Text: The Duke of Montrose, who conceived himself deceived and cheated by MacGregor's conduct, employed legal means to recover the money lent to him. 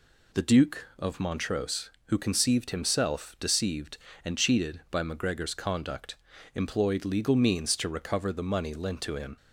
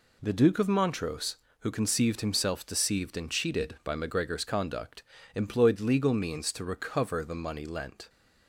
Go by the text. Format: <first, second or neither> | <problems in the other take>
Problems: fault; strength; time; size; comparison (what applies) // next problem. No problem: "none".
first | stops before "to him"; at 8.0 s